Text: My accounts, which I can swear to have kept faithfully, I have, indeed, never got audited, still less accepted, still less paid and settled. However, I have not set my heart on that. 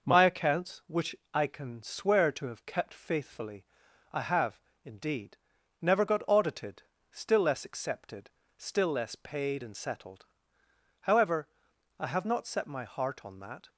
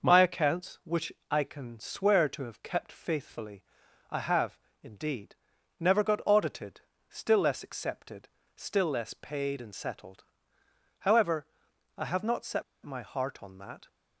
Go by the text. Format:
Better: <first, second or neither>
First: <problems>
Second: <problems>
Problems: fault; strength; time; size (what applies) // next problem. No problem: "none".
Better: first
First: pauses between "which" and "I"; slight; at 1.1 s; 0.18 s long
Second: pauses between "which" and "I"; slight; at 1.1 s; 0.18 s long // pauses between "set" and "my"; slight; at 12.6 s; 0.20 s long